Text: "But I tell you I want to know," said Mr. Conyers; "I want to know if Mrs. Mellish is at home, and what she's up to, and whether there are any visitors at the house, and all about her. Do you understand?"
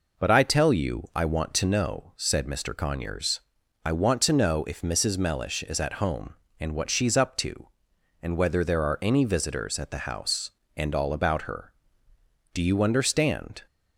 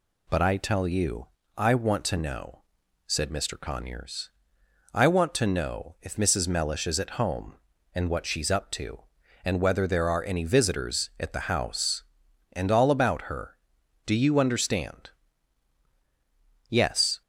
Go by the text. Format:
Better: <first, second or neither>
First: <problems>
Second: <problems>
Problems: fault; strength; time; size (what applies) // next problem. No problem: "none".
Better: first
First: none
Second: pauses between "you" and "I"; slight; at 1.2 s; 0.28 s long // goes on to say "Yes"; from 16.6 s on; 0.54 s long